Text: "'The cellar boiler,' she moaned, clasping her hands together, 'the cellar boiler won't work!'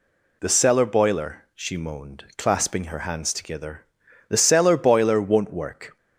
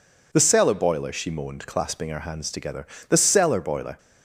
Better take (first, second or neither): first